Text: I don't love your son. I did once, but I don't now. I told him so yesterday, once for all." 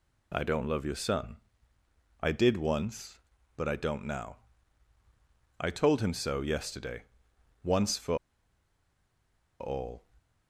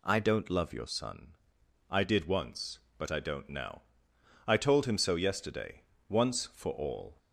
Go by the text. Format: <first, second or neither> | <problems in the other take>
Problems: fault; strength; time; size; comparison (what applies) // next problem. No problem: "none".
second | pauses between "for" and "all"; strong; at 8.1 s; 1.4 s long